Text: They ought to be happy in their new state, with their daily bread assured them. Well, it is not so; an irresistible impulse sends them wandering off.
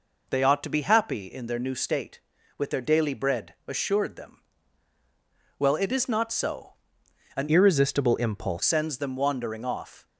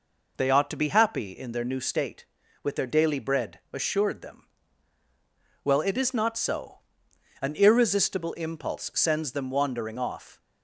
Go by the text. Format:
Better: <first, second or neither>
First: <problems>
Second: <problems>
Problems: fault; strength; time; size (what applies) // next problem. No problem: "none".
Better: second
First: changes voice from "irresistible" to "impulse"; from 7.4 to 8.6 s; 1.2 s long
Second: none